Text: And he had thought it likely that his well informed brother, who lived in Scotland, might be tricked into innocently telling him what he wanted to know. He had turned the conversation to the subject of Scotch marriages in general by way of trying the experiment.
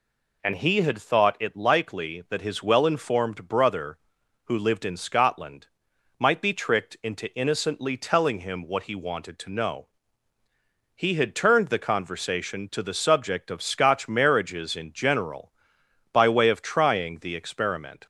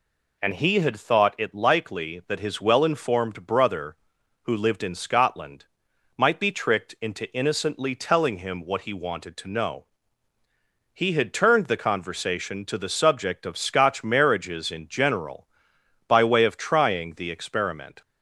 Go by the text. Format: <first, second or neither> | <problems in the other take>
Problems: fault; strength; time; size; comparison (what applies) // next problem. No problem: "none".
neither | none